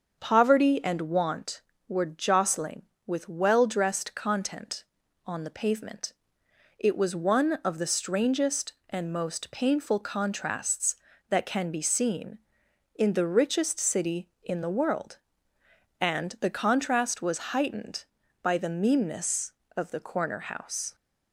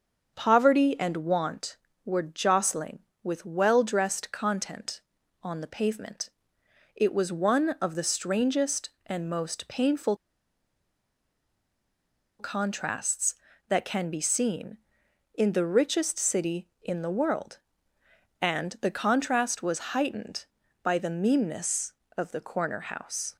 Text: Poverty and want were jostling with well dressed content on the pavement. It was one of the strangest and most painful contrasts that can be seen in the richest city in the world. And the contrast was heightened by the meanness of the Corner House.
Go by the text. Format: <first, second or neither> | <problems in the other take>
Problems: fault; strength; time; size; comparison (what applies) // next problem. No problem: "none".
first | starts louder than the rest; until 1.3 s; 6.5 dB; also in the first // pauses between "painful" and "contrasts"; strong; at 10.1 s; 2.2 s long